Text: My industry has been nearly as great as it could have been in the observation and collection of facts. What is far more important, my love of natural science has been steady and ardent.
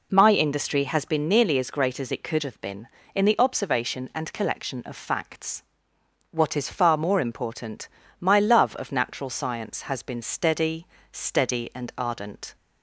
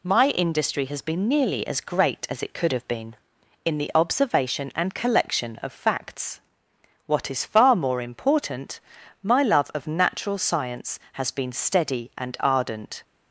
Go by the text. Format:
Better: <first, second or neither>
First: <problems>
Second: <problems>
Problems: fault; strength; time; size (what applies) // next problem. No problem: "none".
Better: second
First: says "steady" twice; at 11.1 s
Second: none